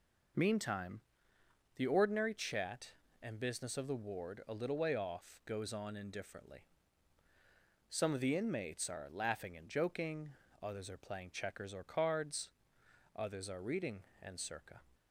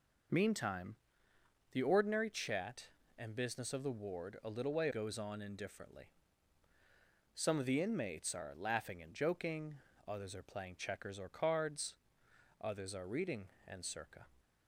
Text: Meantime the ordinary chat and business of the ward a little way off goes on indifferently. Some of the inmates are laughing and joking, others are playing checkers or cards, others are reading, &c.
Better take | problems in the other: first | pauses between "Meantime" and "the"; noticeable; at 0.9 s; 0.78 s long; noticeable in the first // skips "off"; at 4.8 s

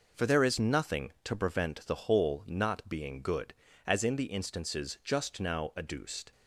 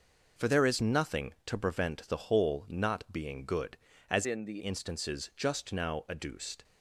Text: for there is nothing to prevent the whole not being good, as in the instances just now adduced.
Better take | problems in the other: first | changes voice from "in" to "the"; from 4.2 to 4.6 s; 0.4 s long

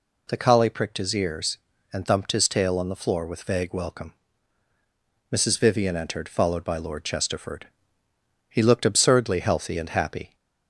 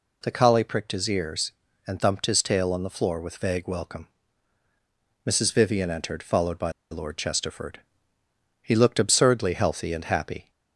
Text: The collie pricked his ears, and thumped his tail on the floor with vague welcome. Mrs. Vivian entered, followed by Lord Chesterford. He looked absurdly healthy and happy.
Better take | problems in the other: first | pauses between "by" and "Lord"; slight; at 6.7 s; 0.19 s long

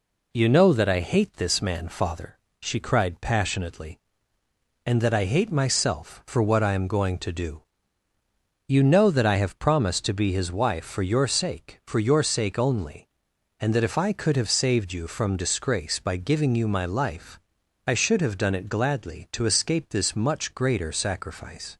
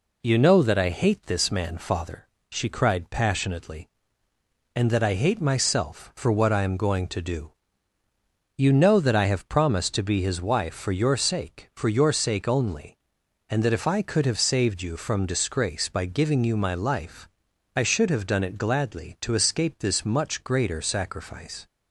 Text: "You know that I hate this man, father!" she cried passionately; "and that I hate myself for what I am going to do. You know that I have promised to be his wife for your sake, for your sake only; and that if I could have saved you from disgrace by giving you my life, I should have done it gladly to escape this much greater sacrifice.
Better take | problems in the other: neither | none

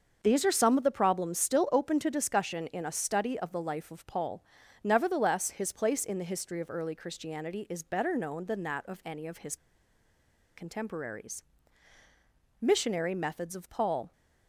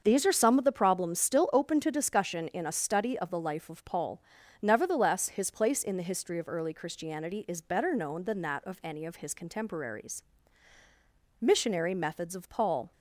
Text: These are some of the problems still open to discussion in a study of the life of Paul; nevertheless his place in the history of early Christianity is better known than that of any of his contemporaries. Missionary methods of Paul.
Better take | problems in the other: second | starts louder than the rest; until 1.2 s; 6.5 dB; also in the second // pauses between "his" and "contemporaries"; at 9.5 s; 1.0 s long

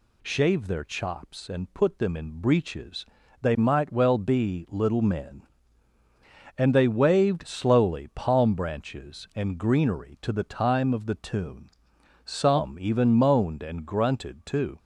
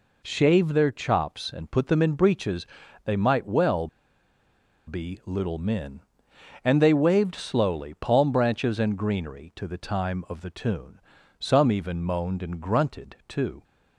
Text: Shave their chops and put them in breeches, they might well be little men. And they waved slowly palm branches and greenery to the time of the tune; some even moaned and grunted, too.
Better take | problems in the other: first | pauses between "well" and "be"; at 3.8 s; 0.99 s long

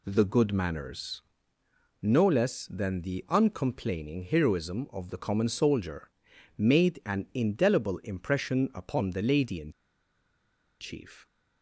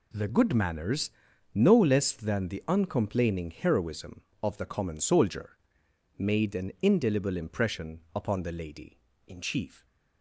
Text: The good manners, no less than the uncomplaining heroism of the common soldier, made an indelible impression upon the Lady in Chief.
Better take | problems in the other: second | pauses between "in" and "Chief"; at 9.7 s; 1.0 s long

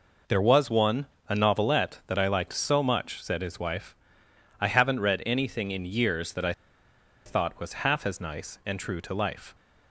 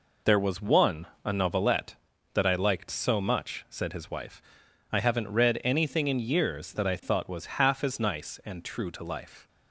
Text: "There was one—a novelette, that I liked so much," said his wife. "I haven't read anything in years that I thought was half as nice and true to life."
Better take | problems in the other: second | pauses between "I" and "thought"; noticeable; at 6.5 s; 0.74 s long

